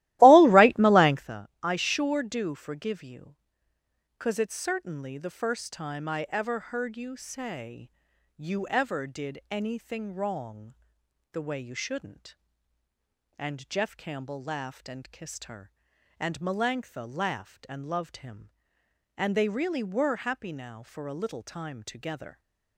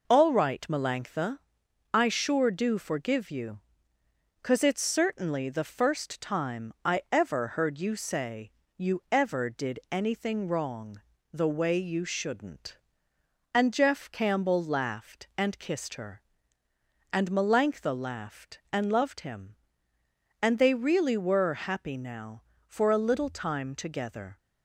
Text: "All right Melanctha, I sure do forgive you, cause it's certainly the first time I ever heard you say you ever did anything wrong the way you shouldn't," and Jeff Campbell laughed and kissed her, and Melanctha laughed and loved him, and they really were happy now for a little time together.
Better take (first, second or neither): second